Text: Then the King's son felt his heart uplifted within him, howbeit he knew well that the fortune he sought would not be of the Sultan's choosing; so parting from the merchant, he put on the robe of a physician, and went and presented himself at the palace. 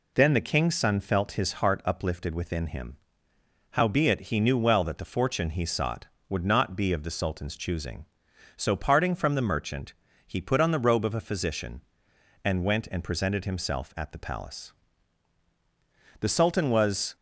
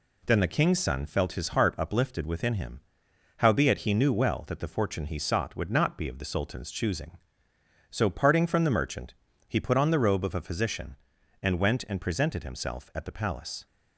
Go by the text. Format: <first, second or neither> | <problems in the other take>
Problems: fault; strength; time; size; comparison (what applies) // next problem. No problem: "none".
second | goes on to say "The Sultan was"; noticeable; from 16.1 s on; 0.96 s long